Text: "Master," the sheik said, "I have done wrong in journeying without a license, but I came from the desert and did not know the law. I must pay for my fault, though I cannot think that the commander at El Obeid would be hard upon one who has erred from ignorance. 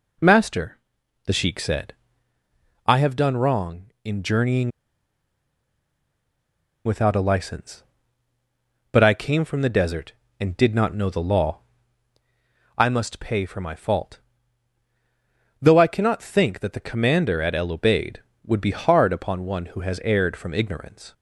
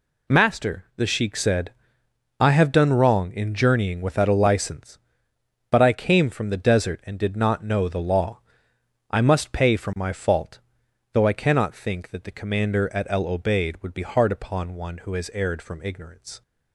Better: second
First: pauses between "journeying" and "without"; strong; at 4.6 s; 2.1 s long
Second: none

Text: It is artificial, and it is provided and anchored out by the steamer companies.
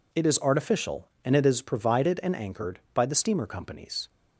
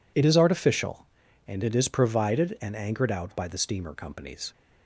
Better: second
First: skips "out"; at 2.8 s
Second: none

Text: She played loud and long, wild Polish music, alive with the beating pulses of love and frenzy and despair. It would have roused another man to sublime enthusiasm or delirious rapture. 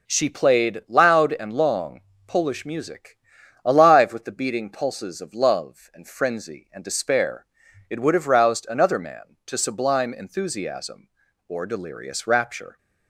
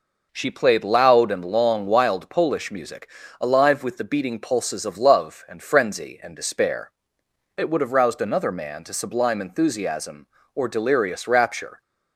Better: second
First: skips "wild"; at 2.1 s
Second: none

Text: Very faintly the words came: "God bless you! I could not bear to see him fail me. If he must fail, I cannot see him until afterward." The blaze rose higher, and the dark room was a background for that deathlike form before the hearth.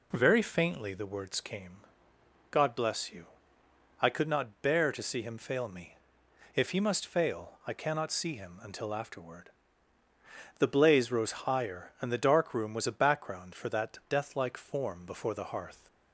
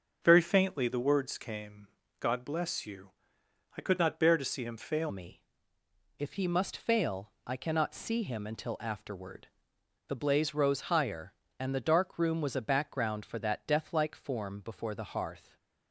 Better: first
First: none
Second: starts louder than the rest; until 1.2 s; 6.5 dB // changes voice at "me"; from 5.0 s on; 10.5 s long // stays silent after the last word; slight; from 15.3 s on; 0.6 s long

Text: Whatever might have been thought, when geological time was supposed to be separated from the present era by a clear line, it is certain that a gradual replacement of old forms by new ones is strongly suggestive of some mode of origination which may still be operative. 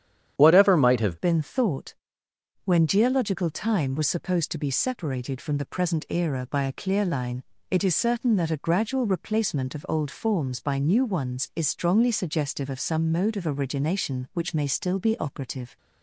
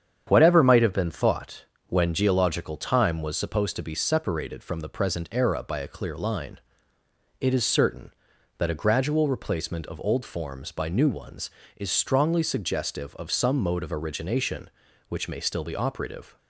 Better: second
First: starts louder than the rest; strong; until 1.3 s; 9.5 dB // changes voice at "been"; from 1.1 s on; 14.6 s long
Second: starts louder than the rest; strong; until 1.2 s; 8 dB

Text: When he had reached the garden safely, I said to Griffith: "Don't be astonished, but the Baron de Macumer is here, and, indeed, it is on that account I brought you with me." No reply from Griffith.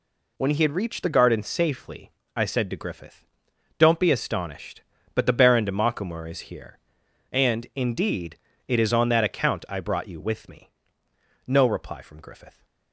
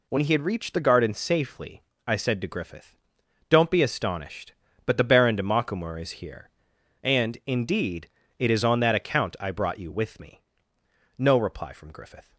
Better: neither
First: none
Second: none

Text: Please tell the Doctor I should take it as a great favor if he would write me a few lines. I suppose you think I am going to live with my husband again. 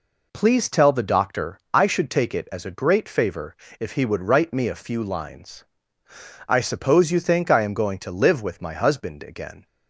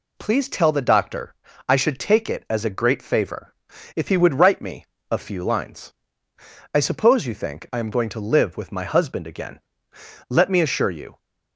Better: first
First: pauses between "Doctor" and "I"; slight; at 1.5 s; 0.16 s long // pauses between "favor" and "if"; slight; at 3.5 s; 0.24 s long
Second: pauses between "Doctor" and "I"; slight; at 1.3 s; 0.32 s long // pauses between "favor" and "if"; at 3.5 s; 0.42 s long // pauses between "me" and "a"; slight; at 4.8 s; 0.28 s long // goes on to say "Let me assure you"; noticeable; from 10.2 s on; 0.90 s long

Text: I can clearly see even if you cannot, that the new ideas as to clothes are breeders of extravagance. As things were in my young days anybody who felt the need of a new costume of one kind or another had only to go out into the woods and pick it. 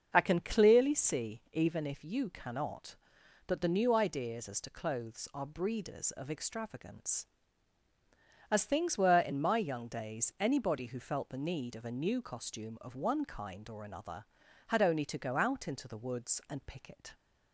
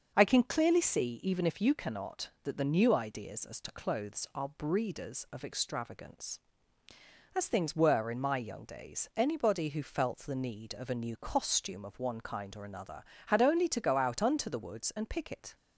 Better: first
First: starts louder than the rest; until 1.1 s; 6.5 dB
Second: starts louder than the rest; noticeable; until 1.1 s; 6 dB // says "unto" for "into"; at 14.2 s

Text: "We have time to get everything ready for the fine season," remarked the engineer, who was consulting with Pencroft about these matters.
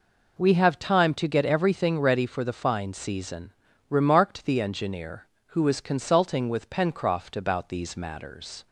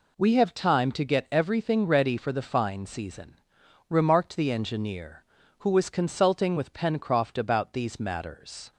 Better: neither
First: none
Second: none

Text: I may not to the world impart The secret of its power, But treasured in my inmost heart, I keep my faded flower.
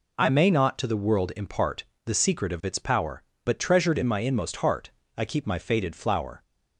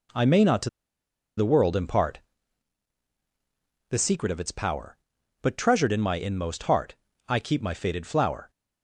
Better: first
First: pauses between "impart" and "The"; slight; at 1.8 s; 0.22 s long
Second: pauses between "to" and "the"; noticeable; at 0.6 s; 0.68 s long // pauses between "impart" and "The"; strong; at 2.2 s; 1.7 s long

